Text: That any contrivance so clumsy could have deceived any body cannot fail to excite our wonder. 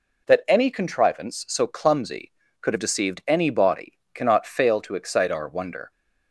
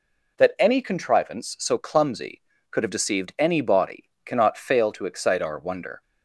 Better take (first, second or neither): neither